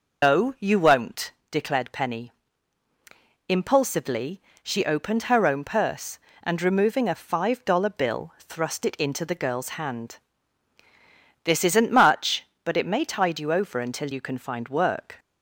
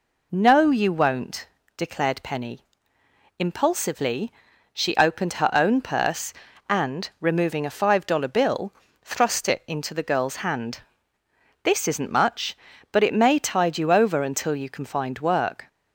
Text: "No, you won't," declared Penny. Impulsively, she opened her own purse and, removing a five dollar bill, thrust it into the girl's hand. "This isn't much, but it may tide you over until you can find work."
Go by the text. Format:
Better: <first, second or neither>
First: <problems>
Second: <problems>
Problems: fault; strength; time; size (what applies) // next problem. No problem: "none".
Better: second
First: loses the start of "No"; at 0.2 s; 145 ms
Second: none